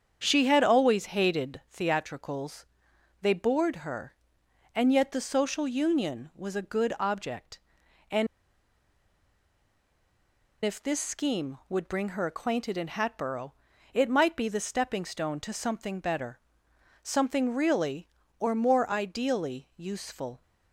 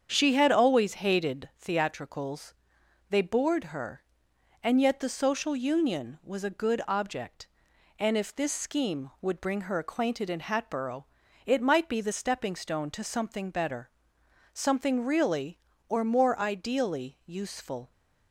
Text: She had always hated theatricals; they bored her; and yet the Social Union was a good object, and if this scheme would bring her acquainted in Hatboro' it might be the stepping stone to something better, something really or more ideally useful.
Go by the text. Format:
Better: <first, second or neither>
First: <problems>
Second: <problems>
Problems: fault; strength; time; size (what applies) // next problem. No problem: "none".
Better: second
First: starts louder than the rest; strong; until 1.2 s; 7.5 dB // pauses between "and" and "if"; strong; at 8.2 s; 2.3 s long // pauses between "Hatboro" and "it"; at 13.5 s; 0.40 s long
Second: starts louder than the rest; strong; until 1.1 s; 7.5 dB // pauses between "Hatboro" and "it"; at 11.0 s; 0.40 s long